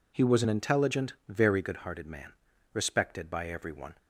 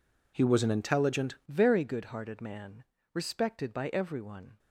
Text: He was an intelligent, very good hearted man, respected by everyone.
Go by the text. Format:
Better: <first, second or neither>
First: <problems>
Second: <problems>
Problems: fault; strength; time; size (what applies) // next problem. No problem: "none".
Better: first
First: none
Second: changes voice at "very"; from 1.4 s on; 3.1 s long